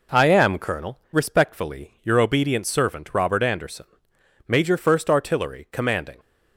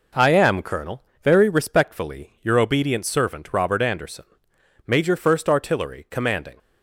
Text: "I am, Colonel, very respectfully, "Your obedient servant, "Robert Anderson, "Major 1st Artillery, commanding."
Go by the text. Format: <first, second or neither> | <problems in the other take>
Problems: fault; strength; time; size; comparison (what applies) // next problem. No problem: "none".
second | skips "very"; at 1.0 s